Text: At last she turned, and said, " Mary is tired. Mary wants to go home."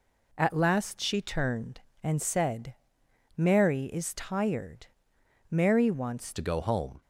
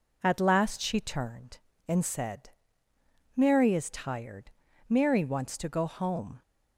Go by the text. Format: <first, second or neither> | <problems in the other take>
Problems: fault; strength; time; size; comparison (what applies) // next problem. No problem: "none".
second | changes voice at "to"; from 6.3 s on; 0.7 s long